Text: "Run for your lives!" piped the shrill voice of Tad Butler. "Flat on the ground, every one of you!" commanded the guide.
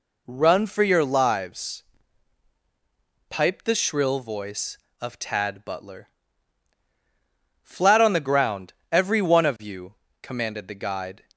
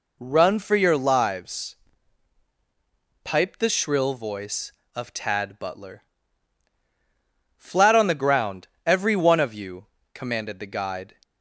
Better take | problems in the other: neither | none

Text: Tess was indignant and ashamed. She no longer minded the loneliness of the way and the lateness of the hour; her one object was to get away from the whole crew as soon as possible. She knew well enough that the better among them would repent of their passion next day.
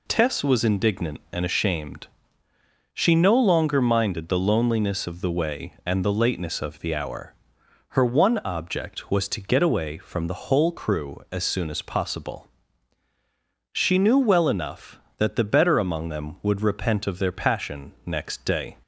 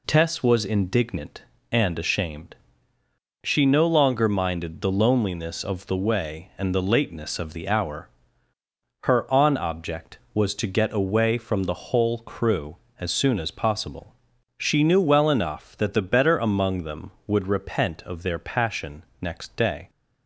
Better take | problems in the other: first | says "on" for "one"; at 9.3 s // pauses between "passion" and "next"; slight; at 19.0 s; 0.18 s long

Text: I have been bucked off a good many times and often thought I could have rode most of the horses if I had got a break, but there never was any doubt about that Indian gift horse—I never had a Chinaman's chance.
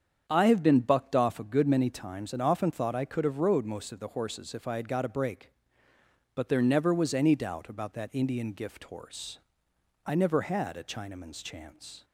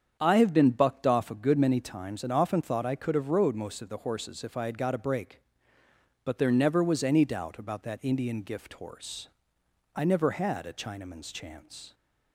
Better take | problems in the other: neither | starts louder than the rest; strong; the same in both

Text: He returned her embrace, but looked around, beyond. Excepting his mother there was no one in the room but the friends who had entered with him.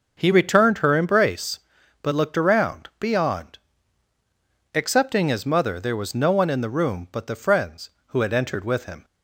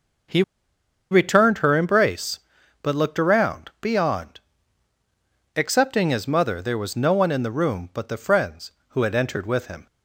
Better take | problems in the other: first | pauses between "He" and "returned"; noticeable; at 0.4 s; 0.67 s long

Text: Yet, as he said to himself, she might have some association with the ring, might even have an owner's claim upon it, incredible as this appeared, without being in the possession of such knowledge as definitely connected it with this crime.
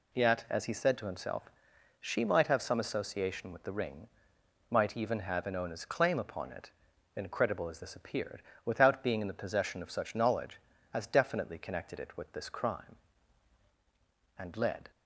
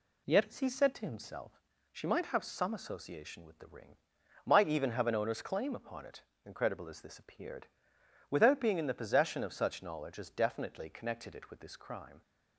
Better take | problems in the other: second | goes on to say "And led"; from 14.3 s on; 0.52 s long

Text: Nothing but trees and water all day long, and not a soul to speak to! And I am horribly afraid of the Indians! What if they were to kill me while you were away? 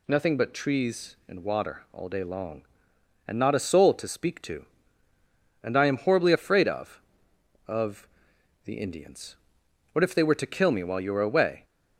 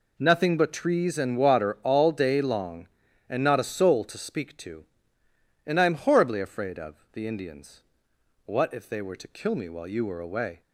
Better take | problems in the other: second | says "of" twice; at 7.6 s

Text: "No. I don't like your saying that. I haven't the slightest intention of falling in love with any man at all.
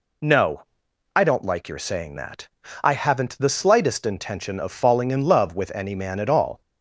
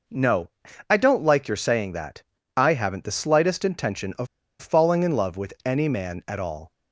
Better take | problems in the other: first | pauses between "of" and "falling"; slight; at 4.2 s; 0.33 s long

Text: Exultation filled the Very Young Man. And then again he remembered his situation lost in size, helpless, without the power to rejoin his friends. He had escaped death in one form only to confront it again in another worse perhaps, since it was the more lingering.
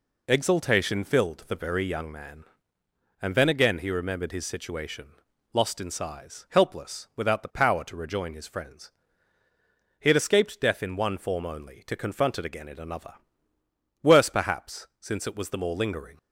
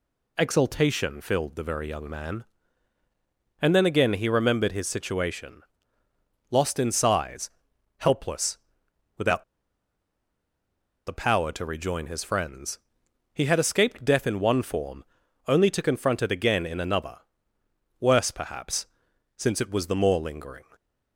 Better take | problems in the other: first | pauses between "situation" and "lost"; noticeable; at 5.6 s; 0.92 s long; noticeable in the first // pauses between "without" and "the"; strong; at 9.4 s; 1.6 s long // pauses between "form" and "only"; at 15.0 s; 0.44 s long // pauses between "another" and "worse"; noticeable; at 17.1 s; 0.84 s long; noticeable in the first

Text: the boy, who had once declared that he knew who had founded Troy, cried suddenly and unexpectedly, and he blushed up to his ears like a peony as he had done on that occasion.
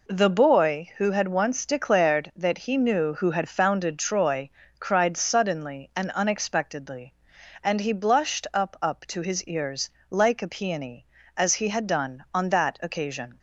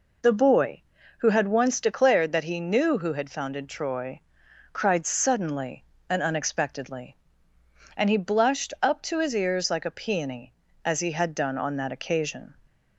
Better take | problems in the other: second | says "up" twice; at 8.7 s // pauses between "ears" and "like"; slight; at 9.8 s; 0.18 s long

